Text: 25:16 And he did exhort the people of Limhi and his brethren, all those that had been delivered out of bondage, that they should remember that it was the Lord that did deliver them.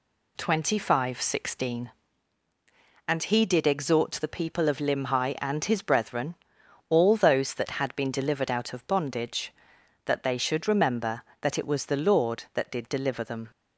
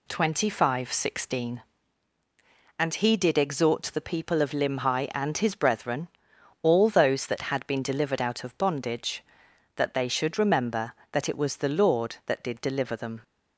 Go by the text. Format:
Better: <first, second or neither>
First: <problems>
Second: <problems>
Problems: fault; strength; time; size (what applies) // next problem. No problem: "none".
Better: neither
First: none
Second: none